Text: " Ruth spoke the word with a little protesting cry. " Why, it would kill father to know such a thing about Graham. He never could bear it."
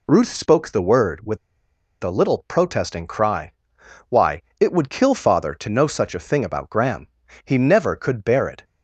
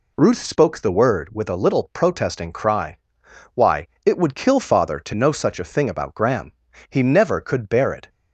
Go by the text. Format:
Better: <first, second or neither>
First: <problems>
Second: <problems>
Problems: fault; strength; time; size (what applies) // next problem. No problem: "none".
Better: second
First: pauses between "with" and "a"; noticeable; at 1.3 s; 0.66 s long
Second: none